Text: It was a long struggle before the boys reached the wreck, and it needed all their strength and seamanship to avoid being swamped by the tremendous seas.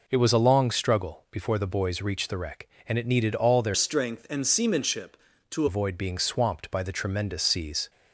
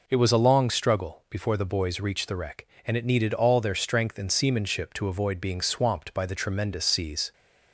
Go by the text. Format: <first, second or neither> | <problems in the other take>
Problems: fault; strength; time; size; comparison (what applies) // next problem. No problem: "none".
second | changes voice from "strength" to "to"; from 3.7 to 5.6 s; 1.9 s long